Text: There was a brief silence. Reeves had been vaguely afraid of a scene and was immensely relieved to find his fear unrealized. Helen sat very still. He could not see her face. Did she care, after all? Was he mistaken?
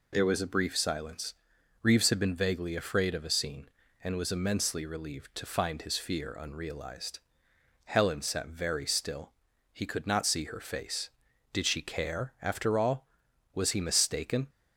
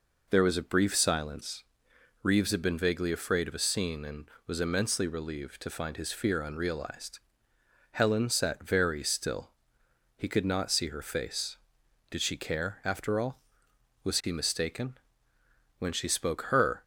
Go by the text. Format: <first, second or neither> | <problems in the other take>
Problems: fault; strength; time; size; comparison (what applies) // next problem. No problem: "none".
first | goes on to say "When she spoke her"; noticeable; from 15.7 s on; 1.0 s long